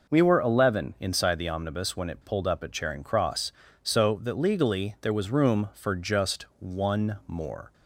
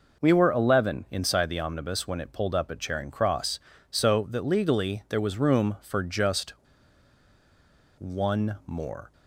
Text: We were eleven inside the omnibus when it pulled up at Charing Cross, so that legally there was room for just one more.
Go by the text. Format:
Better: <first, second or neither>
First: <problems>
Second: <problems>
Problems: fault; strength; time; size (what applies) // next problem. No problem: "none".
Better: first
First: none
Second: pauses between "just" and "one"; strong; at 6.5 s; 1.4 s long